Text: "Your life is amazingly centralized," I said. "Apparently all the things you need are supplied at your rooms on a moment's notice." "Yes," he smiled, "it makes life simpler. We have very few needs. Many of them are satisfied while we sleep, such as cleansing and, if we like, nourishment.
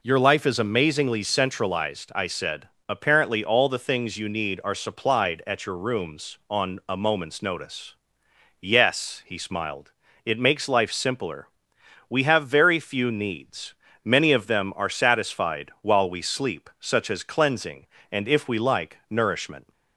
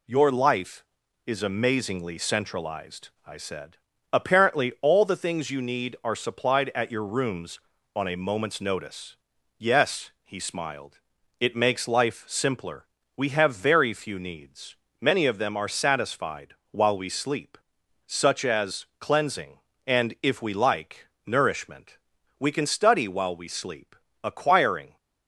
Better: first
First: none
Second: pauses between "satisfied" and "while"; slight; at 16.5 s; 0.16 s long // goes on to say "We can study while we sleep acquiring"; strong; from 22.4 s on; 2.5 s long

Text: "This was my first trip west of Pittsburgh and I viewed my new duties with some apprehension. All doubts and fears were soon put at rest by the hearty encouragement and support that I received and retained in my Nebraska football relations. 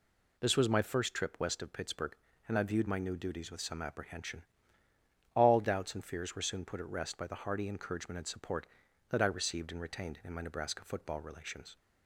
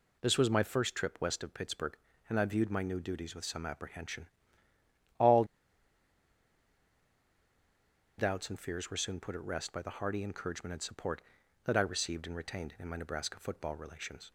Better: first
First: none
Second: pauses between "All" and "doubts"; strong; at 5.4 s; 2.7 s long

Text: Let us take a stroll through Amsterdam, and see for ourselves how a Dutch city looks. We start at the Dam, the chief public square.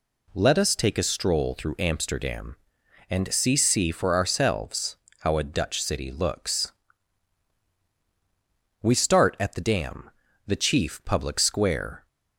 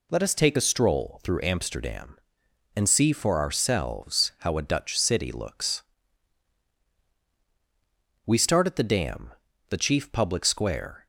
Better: second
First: says "see" twice; at 3.5 s // pauses between "ourselves" and "how"; slight; at 4.9 s; 0.26 s long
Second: none

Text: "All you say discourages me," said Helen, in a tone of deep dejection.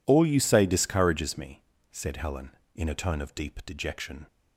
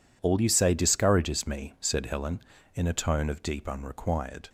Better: first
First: none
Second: says "unrequired" for "dejection"; at 3.6 s

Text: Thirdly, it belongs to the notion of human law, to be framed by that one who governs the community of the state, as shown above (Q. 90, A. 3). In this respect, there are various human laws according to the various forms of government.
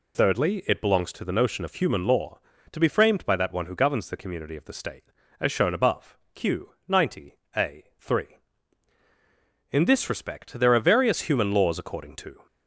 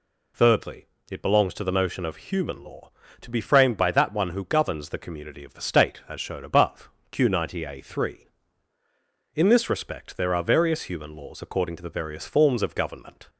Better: second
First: stops before "the various forms of government"; at 12.4 s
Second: none

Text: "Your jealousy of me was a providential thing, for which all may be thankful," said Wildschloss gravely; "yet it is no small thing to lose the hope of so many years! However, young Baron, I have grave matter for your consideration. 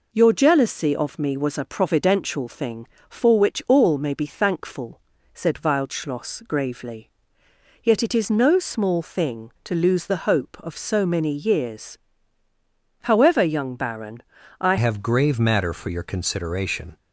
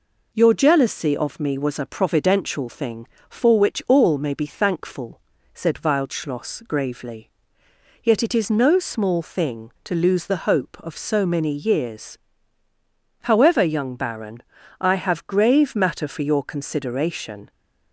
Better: second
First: changes voice at "have"; from 14.7 s on; 2.2 s long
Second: none

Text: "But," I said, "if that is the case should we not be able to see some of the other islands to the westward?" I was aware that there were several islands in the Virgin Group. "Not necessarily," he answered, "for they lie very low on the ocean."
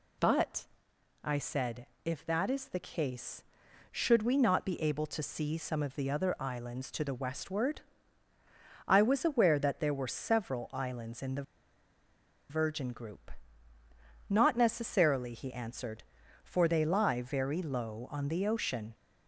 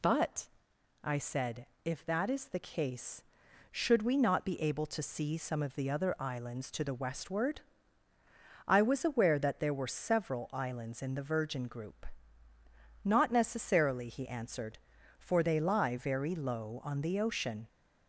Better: second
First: pauses between "the" and "Virgin"; at 11.4 s; 1.0 s long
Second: none

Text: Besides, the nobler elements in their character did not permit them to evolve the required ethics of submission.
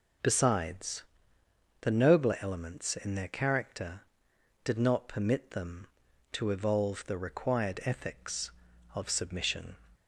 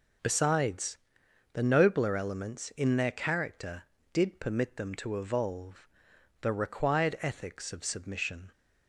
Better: first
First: none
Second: skips "not"; at 4.4 s // pauses between "evolve" and "the"; noticeable; at 5.8 s; 0.54 s long

